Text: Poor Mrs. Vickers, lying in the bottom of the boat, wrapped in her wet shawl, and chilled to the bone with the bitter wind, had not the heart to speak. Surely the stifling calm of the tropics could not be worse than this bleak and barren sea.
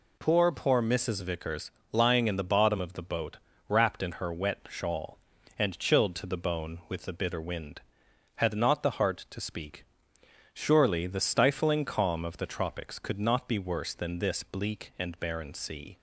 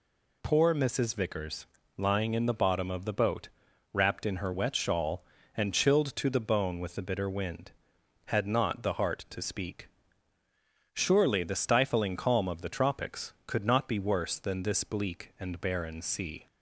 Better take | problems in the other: second | says "Poor" twice; at 0.4 s

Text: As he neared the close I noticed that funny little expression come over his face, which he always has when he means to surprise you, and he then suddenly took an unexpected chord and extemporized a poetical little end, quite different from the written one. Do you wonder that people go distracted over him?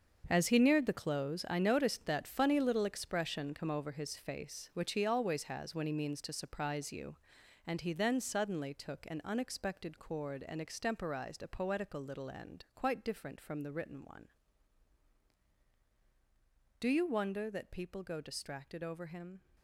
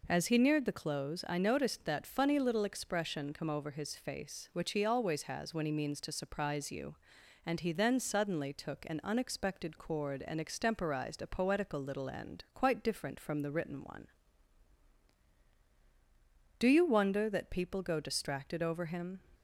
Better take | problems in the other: second | gets quieter; strong; throughout; 12 dB

